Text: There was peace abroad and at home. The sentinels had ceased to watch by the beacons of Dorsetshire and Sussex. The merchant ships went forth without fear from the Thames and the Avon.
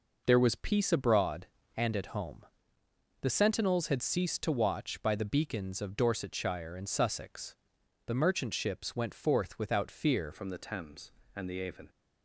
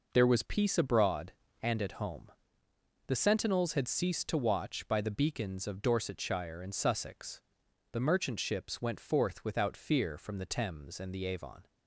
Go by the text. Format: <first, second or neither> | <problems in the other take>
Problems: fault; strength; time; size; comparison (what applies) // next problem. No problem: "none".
second | changes voice at "from"; from 10.3 s on; 1.5 s long